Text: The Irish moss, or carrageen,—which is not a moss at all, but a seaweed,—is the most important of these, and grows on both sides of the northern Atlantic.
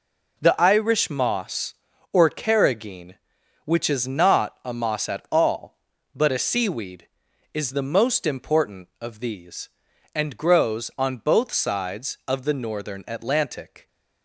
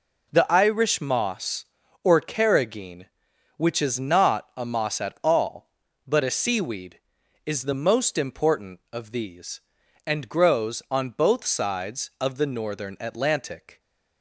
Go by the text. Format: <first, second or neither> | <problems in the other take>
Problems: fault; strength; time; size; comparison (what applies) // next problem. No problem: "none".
neither | none